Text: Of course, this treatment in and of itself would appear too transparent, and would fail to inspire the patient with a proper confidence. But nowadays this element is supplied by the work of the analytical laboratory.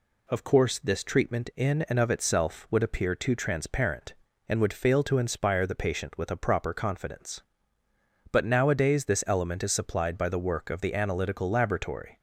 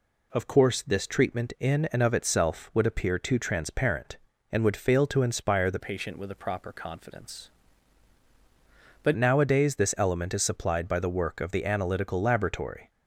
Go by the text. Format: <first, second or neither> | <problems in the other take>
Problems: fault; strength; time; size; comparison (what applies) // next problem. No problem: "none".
first | changes voice from "patient" to "But"; from 5.8 to 9.1 s; 3.3 s long